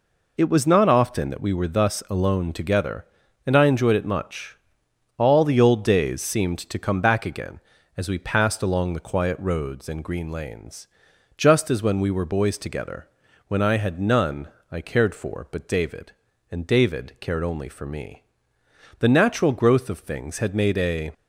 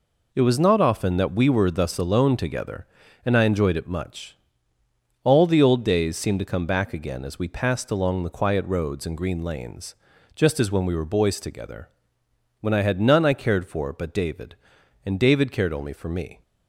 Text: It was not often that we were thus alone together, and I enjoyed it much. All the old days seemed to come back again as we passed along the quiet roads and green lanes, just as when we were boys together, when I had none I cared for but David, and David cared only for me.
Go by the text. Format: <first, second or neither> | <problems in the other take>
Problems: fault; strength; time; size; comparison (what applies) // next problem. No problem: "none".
second | pauses between "none" and "I"; slight; at 14.4 s; 0.22 s long // goes on to say "The natural growth of things had made a"; strong; from 18.9 s on; 2.1 s long